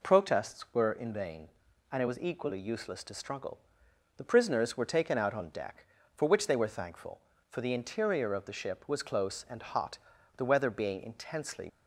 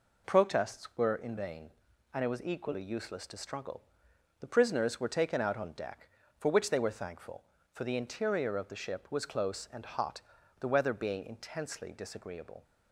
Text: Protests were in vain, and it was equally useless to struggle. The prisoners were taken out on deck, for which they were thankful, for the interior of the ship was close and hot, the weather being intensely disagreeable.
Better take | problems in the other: second | stops before "disagreeable"; at 11.6 s

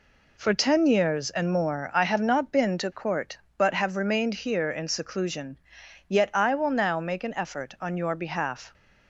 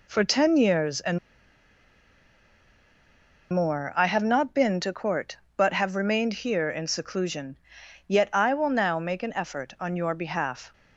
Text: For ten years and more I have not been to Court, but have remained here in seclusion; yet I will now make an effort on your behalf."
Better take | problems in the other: first | pauses between "and" and "more"; strong; at 1.1 s; 2.3 s long

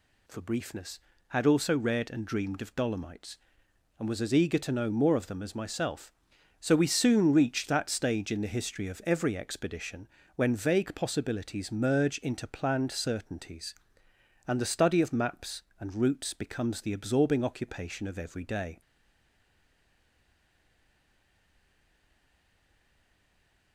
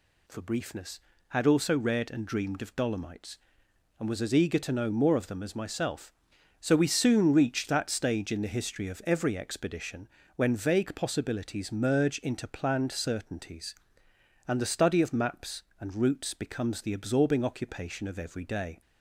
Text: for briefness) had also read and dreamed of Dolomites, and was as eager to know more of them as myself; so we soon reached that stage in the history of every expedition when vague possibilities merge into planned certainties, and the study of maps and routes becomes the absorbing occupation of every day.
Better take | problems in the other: second | pauses between "expedition" and "when"; slight; at 10.0 s; 0.26 s long; slight in the second // stays silent after the last word; strong; from 18.8 s on; 4.9 s long

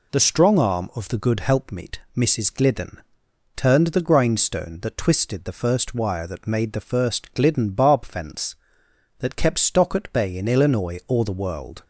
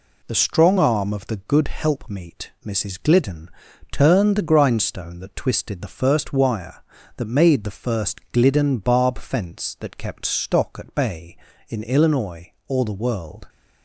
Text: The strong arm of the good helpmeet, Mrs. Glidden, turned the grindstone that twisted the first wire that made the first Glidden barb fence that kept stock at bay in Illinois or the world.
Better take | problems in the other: neither | none

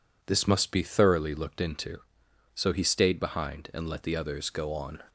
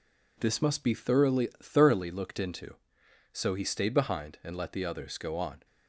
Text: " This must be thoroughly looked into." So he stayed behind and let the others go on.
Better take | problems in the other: first | says "thoroughly" twice; at 1.6 s

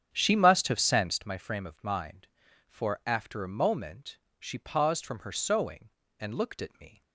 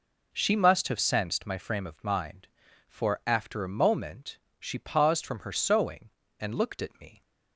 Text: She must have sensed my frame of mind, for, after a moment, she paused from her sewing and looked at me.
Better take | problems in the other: second | starts louder than the rest; strong; until 1.3 s; 8.5 dB

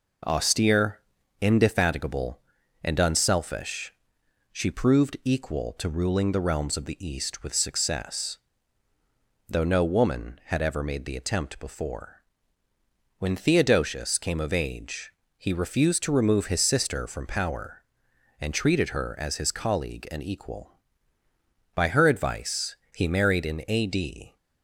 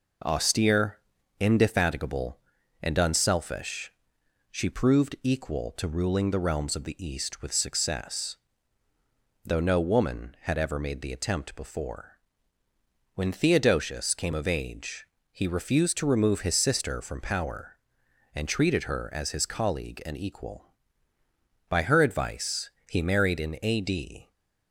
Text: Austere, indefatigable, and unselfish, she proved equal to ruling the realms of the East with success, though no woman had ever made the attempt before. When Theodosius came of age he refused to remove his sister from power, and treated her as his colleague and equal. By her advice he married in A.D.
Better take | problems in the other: neither | pauses between "age" and "he"; slight; the same in both // pauses between "advice" and "he"; slight; the same in both

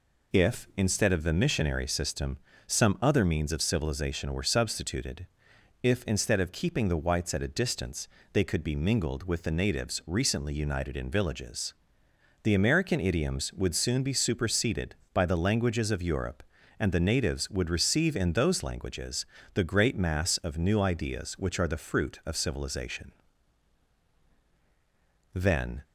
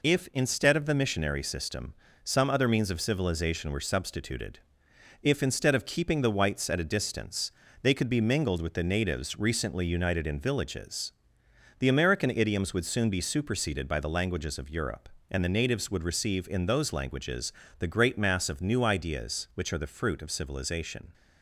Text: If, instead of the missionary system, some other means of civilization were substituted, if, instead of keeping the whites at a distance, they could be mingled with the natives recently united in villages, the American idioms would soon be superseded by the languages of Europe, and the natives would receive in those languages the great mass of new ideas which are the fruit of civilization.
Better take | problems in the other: second | pauses between "languages" and "the"; slight; at 19.2 s; 0.26 s long; slight in the second // goes on to say "Then"; slight; from 25.3 s on; 0.48 s long

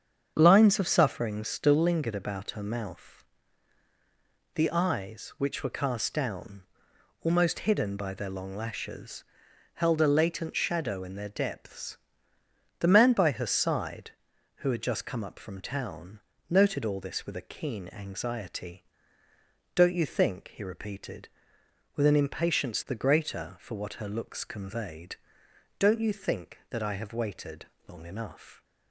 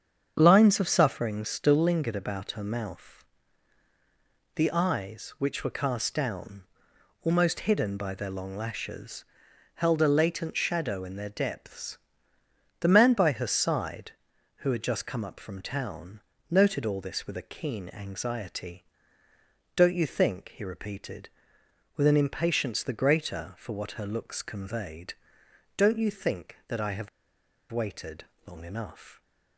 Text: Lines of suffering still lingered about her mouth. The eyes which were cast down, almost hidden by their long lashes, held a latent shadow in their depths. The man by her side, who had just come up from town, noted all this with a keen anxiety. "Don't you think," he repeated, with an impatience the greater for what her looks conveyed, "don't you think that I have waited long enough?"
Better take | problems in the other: first | starts louder than the rest; strong; until 1.3 s; 7 dB; strong in the first // pauses between "have" and "waited"; noticeable; at 27.0 s; 0.63 s long // pauses between "waited" and "long"; slight; at 28.2 s; 0.22 s long; slight in the first

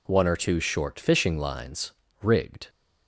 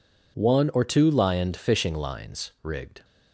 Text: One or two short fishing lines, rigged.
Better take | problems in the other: first | says "lioned" for "short"; at 1.1 s

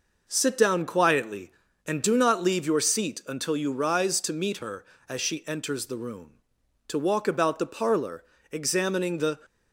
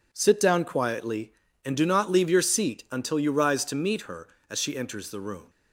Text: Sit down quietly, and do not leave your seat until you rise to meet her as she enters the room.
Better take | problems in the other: second | goes on to say "To walk about the parlor examining the"; strong; from 6.8 s on; 2.5 s long

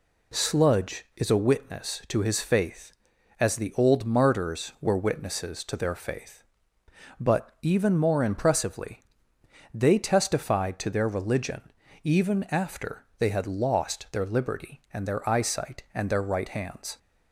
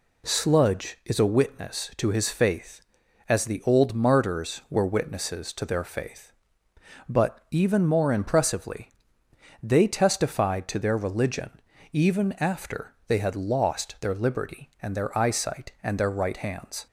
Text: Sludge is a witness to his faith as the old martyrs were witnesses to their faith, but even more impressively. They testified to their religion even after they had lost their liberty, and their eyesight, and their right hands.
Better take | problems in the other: neither | pauses between "religion" and "even"; the same in both

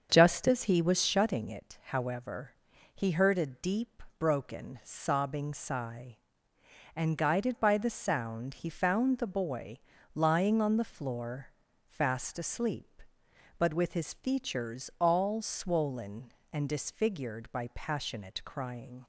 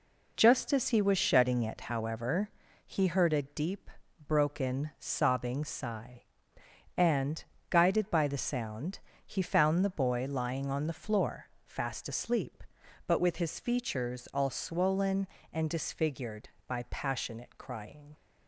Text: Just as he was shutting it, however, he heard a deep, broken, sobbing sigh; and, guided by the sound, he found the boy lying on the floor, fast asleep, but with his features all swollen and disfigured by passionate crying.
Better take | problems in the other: second | starts louder than the rest; until 1.3 s; 7 dB // pauses between "boy" and "lying"; slight; at 9.7 s; 0.34 s long

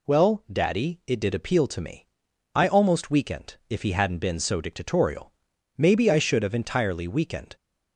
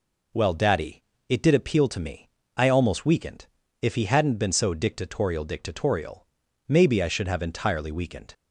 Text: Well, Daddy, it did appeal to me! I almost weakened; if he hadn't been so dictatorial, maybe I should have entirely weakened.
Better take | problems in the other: first | says "dictatorial" twice; at 5.4 s

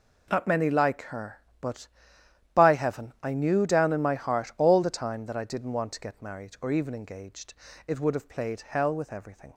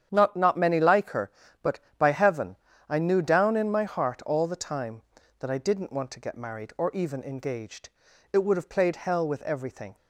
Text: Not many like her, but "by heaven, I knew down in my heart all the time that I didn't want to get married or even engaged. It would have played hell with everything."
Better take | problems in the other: first | starts louder than the rest; strong; until 1.1 s; 9 dB // says "Not" twice; at 0.3 s

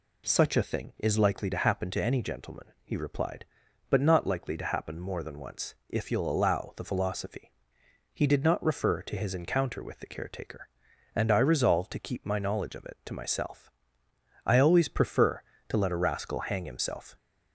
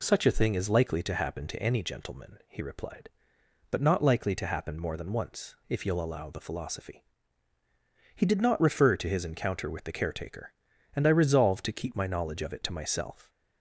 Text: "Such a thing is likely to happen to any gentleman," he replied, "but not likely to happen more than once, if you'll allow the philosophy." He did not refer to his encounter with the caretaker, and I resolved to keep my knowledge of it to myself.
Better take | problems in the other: second | goes on to say "I always prefer to let a rascal hang himself"; strong; from 14.4 s on; 2.7 s long

